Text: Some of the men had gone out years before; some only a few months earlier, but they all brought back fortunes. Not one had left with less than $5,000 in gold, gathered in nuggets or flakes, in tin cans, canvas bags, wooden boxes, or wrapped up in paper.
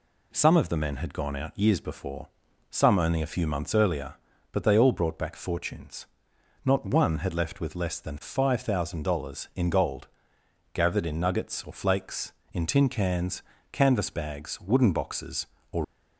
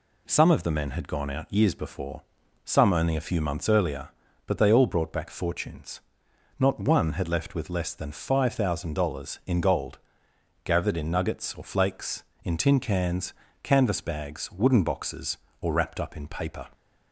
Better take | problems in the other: second | stops before "wrapped up in paper"; at 15.8 s

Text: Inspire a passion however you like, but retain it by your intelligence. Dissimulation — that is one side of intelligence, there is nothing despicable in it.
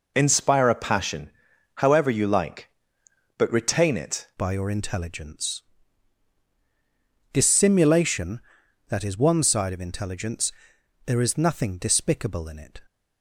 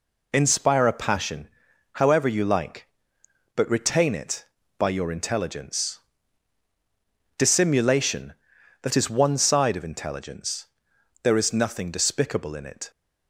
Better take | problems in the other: second | pauses between "passion" and "however"; noticeable; at 1.2 s; 0.46 s long; noticeable in the second // changes voice at "by"; from 4.3 s on; 8.5 s long

